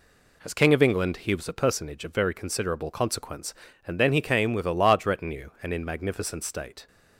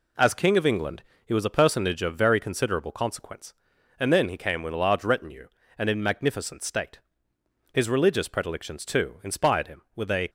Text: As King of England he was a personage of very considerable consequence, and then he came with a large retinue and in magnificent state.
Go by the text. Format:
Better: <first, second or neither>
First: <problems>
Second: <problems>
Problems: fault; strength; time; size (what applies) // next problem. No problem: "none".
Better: first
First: none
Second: pauses between "England" and "he"; slight; at 1.0 s; 0.24 s long // goes on to say "His religious predilections too inspired him with a"; strong; from 7.7 s on; 2.5 s long